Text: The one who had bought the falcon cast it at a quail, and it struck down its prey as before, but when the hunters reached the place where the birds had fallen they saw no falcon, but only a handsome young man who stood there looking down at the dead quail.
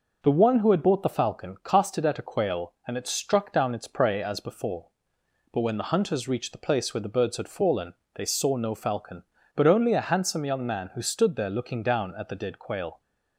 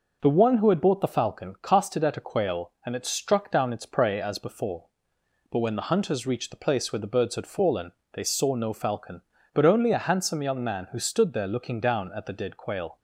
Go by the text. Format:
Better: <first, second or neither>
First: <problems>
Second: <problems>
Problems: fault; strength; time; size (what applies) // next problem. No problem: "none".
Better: neither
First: pauses between "fallen" and "they"; slight; at 7.9 s; 0.20 s long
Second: pauses between "fallen" and "they"; slight; at 7.9 s; 0.20 s long